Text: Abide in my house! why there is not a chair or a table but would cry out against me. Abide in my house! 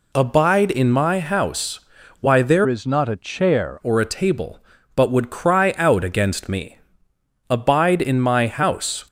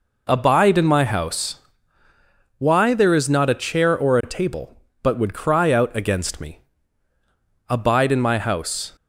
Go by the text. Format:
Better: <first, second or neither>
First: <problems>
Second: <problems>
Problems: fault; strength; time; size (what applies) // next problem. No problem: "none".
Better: second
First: changes voice from "is" to "chair"; from 2.6 to 3.7 s; 1.1 s long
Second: none